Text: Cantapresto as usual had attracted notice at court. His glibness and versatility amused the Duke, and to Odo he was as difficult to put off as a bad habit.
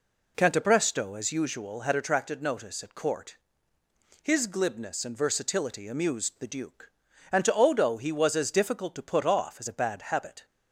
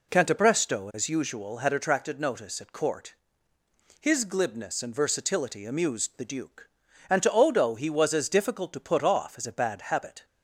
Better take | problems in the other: neither | none

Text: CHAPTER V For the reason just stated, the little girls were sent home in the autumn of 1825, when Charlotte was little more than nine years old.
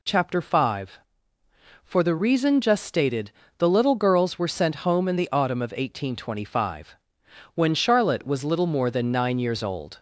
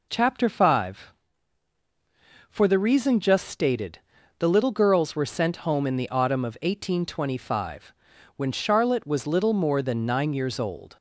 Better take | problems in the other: neither | none

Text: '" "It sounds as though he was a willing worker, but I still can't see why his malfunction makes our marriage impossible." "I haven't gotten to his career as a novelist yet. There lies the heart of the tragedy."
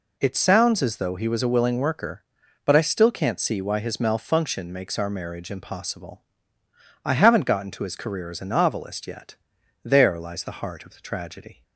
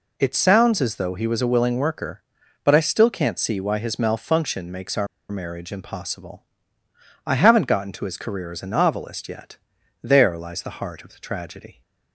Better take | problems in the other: first | pauses between "our" and "marriage"; slight; at 5.0 s; 0.24 s long

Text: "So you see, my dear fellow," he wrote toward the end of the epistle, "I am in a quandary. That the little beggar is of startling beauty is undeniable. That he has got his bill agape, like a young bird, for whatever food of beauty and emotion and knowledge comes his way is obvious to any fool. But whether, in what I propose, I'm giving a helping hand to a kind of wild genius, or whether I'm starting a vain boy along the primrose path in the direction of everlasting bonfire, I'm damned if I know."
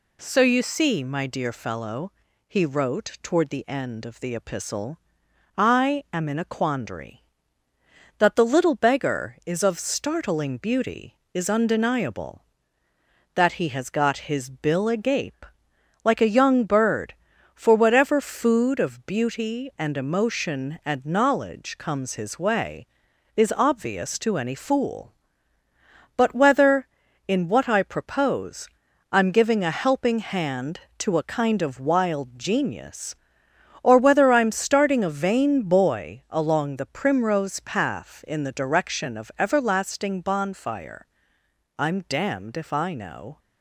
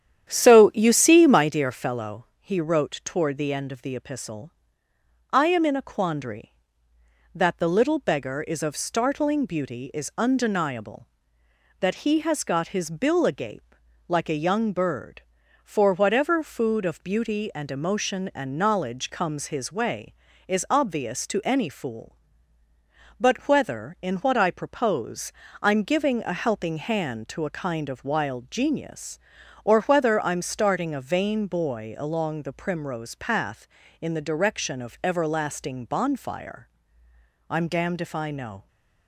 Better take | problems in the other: first | starts louder than the rest; strong; until 1.5 s; 10 dB

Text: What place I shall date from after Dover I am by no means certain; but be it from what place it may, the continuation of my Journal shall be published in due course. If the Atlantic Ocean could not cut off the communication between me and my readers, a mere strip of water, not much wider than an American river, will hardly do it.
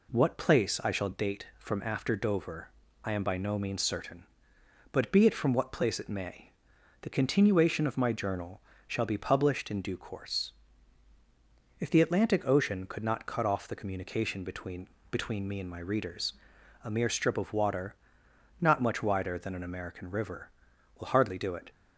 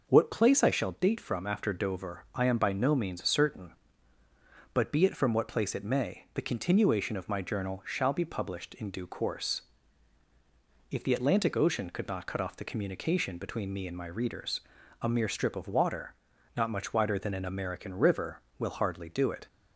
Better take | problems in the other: second | pauses between "Dover" and "I"; slight; at 2.6 s; 0.34 s long // pauses between "Journal" and "shall"; slight; at 8.5 s; 0.28 s long // says "between" twice; at 15.1 s

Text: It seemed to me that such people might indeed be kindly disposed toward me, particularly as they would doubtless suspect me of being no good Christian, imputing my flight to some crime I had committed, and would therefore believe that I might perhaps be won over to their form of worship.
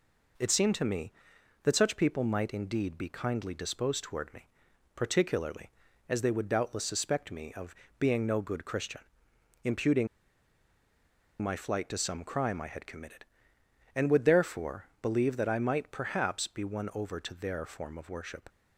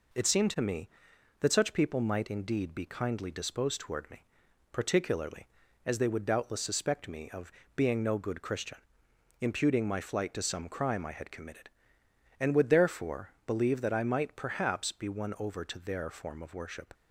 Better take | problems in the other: second | pauses between "of" and "being"; slight; at 7.7 s; 0.24 s long; slight in the second // pauses between "imputing" and "my"; strong; at 10.0 s; 1.3 s long

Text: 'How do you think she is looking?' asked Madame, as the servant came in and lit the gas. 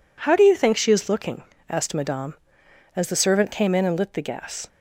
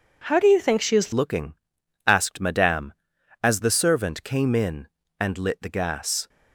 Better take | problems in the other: first | changes voice at "looking"; from 1.1 s on; 5.1 s long

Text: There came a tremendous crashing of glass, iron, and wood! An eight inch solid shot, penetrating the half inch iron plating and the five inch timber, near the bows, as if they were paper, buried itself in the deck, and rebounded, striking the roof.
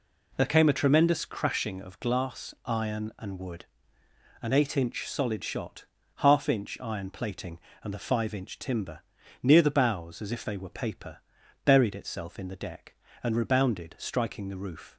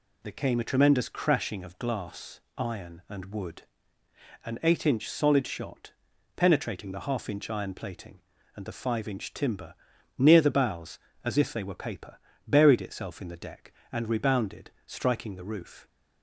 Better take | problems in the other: second | skips "penetrating the"; at 6.0 s

